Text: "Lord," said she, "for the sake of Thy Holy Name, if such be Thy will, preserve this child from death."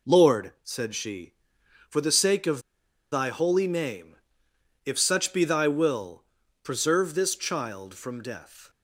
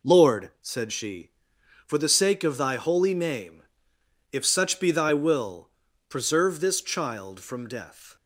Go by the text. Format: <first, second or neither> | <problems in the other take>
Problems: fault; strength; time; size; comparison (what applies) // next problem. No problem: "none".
second | pauses between "of" and "Thy"; noticeable; at 2.5 s; 0.52 s long